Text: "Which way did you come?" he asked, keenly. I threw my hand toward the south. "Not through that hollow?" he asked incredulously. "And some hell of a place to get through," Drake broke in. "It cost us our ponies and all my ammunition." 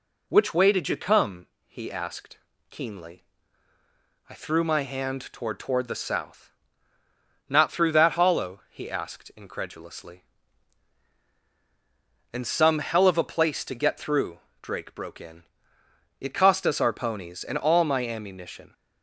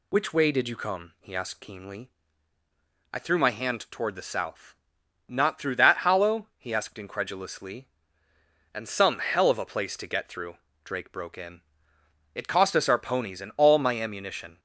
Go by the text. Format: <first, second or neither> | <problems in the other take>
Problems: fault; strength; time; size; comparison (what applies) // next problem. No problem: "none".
second | says "toward" twice; at 5.5 s